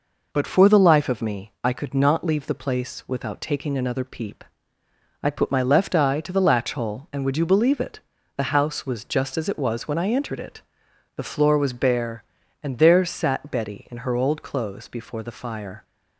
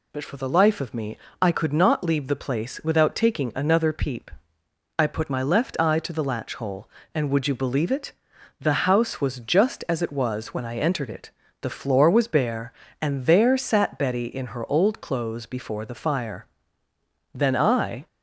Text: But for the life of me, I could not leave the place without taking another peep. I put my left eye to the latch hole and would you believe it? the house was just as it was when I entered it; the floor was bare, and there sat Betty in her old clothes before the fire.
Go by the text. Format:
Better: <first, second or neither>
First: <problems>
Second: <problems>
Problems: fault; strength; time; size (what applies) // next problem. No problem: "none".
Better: first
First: none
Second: goes on to say "Then I"; noticeable; from 17.3 s on; 0.72 s long